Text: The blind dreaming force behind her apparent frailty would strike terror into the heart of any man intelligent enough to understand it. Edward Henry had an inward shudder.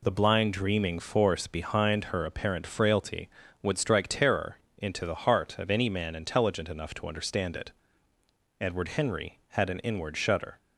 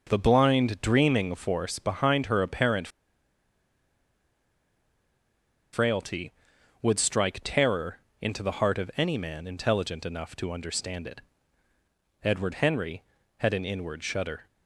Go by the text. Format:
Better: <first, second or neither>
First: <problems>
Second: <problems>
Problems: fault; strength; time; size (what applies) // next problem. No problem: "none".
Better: first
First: pauses between "terror" and "into"; slight; at 4.5 s; 0.20 s long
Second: pauses between "apparent" and "frailty"; strong; at 2.8 s; 2.8 s long // pauses between "terror" and "into"; slight; at 7.9 s; 0.20 s long